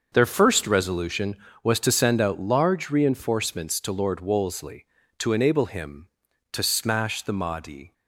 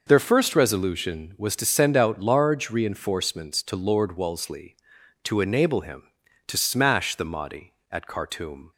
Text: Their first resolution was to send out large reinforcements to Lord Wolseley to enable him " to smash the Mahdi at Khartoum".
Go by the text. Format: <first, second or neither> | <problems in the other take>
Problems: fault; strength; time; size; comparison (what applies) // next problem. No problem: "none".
second | starts louder than the rest; until 1.1 s; 6.5 dB // stops before "at Khartoum"; at 7.9 s